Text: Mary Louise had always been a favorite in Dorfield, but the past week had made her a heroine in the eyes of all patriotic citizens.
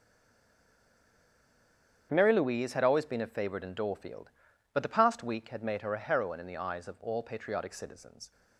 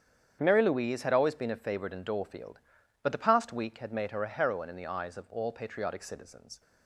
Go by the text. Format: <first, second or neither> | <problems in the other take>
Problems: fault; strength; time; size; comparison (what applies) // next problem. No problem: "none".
second | stays silent before the first word; noticeable; until 2.1 s; 2.1 s long // starts louder than the rest; strong; until 3.1 s; 8 dB; strong in the second